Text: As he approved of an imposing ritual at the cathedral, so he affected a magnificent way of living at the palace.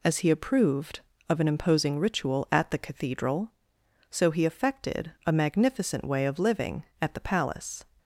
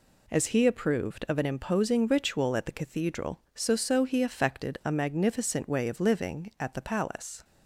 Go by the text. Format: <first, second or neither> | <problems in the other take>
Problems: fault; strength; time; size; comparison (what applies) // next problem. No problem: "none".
first | says "so" twice; at 3.7 s